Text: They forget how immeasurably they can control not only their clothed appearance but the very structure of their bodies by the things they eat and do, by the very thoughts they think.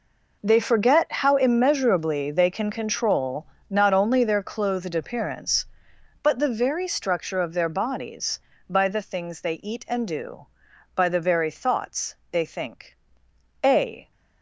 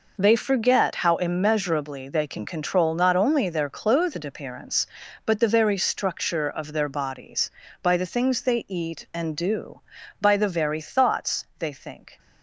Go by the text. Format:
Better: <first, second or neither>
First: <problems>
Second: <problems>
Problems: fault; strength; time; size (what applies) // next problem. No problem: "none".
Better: second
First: pauses between "control" and "not"; slight; at 3.4 s; 0.26 s long // pauses between "thoughts" and "they"; slight; at 12.1 s; 0.18 s long // goes on to say "A"; slight; from 13.6 s on; 0.46 s long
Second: none